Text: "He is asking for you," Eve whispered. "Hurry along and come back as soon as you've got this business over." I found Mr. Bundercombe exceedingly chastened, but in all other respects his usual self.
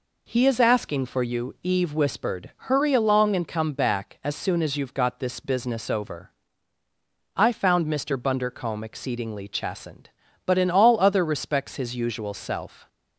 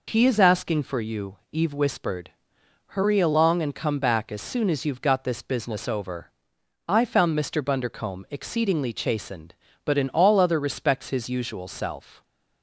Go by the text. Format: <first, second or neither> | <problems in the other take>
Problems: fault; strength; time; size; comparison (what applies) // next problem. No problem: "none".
neither | none